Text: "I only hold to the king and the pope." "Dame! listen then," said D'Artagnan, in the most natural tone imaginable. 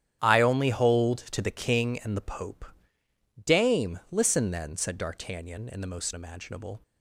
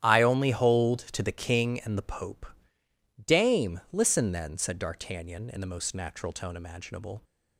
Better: second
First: starts louder than the rest; strong; until 1.3 s; 10.5 dB // skips "natural tone"; at 6.1 s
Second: starts louder than the rest; strong; until 1.1 s; 11 dB

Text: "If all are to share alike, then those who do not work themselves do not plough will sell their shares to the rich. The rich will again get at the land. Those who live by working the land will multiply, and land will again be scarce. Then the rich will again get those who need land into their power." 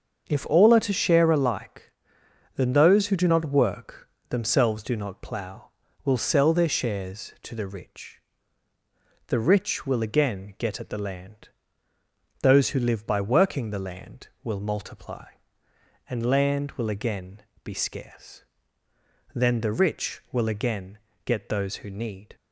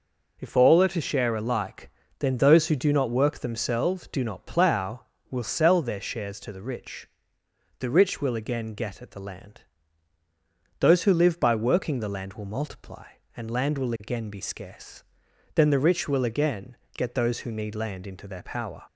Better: second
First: starts louder than the rest; until 1.3 s; 6.5 dB // pauses between "work" and "themselves"; slight; at 4.0 s; 0.22 s long // pauses between "again" and "be"; slight; at 17.4 s; 0.22 s long // pauses between "again" and "get"; slight; at 20.9 s; 0.26 s long // stops before "land into their power"; at 22.3 s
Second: pauses between "again" and "get"; slight; at 16.7 s; 0.18 s long

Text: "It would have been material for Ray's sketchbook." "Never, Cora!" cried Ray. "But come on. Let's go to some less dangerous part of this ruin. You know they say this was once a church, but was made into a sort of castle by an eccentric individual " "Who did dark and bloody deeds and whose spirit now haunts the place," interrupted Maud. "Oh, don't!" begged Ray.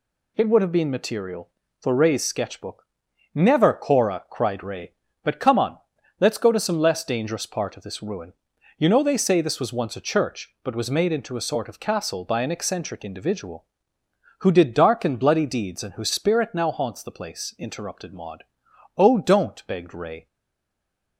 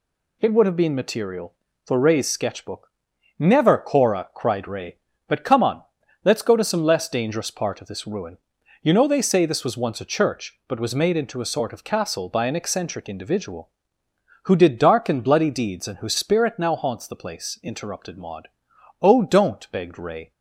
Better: second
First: stays silent after the last word; from 20.2 s on; 0.9 s long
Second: none

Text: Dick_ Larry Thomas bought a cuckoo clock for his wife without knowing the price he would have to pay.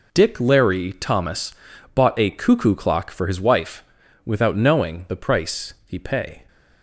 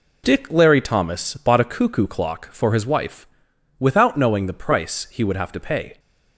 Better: second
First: pauses between "Thomas" and "bought"; at 1.5 s; 0.40 s long // pauses between "wife" and "without"; at 3.8 s; 0.42 s long // skips "would have to"; at 5.9 s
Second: pauses between "wife" and "without"; noticeable; at 3.2 s; 0.52 s long

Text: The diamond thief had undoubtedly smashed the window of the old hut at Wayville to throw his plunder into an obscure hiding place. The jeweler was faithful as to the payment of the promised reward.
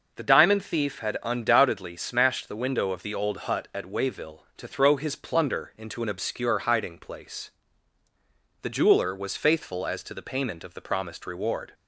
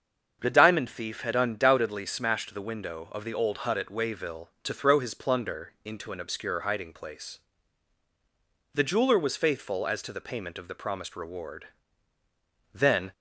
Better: first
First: none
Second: starts louder than the rest; until 1.4 s; 7 dB // goes on to say "Then"; slight; from 12.7 s on; 0.40 s long

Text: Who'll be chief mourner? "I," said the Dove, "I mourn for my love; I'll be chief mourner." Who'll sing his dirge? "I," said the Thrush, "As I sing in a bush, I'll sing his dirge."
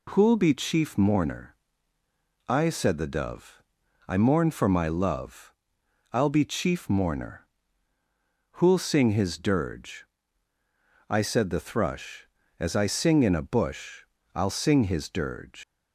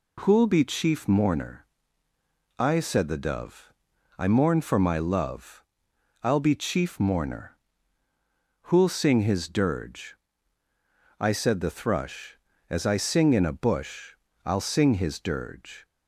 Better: second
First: leaves "dirge" unfinished; at 15.6 s; 130 ms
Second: none

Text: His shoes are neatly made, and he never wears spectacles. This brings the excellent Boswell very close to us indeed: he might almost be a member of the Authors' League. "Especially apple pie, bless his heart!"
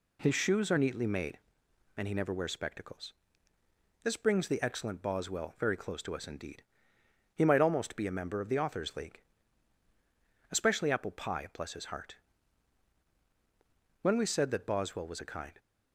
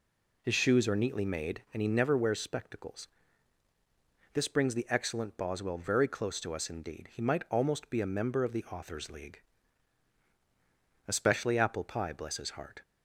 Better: second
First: goes on to say "When we said that Boswell was a kind"; from 14.0 s on; 1.5 s long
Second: none

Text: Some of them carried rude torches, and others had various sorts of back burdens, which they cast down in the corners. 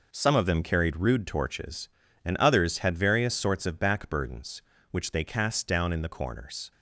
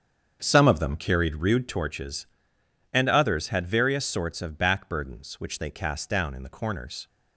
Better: first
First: none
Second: starts louder than the rest; strong; until 1.9 s; 7 dB

